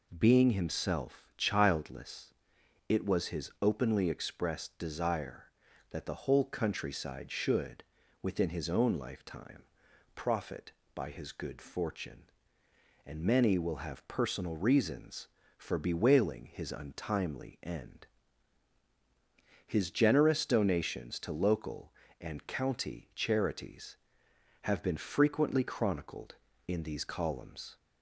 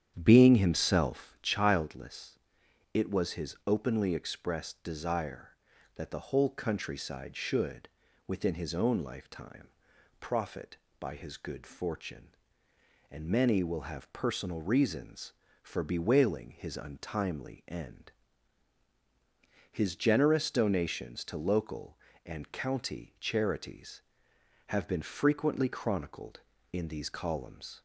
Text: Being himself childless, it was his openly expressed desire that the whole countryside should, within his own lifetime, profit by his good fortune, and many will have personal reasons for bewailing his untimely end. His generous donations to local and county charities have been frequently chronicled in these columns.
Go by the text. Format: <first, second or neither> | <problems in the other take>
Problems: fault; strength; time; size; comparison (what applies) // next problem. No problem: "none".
first | starts louder than the rest; strong; until 1.5 s; 9.5 dB